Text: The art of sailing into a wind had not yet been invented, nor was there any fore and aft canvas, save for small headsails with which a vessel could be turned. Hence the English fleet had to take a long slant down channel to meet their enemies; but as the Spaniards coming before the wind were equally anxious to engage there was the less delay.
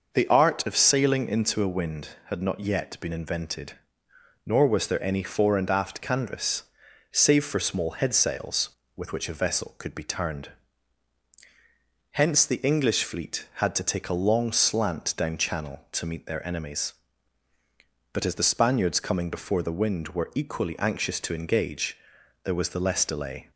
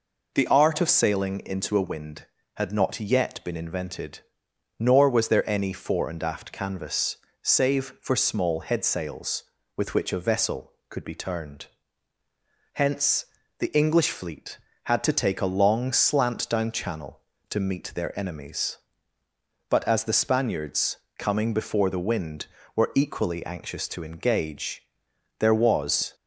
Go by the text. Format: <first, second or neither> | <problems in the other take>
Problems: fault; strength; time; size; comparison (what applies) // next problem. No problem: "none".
first | pauses between "Hence" and "the"; slight; at 13.2 s; 0.32 s long // pauses between "Spaniards" and "coming"; slight; at 20.9 s; 0.22 s long // pauses between "engage" and "there"; noticeable; at 24.8 s; 0.56 s long; noticeable in the first // stops before "the less delay"; at 26.1 s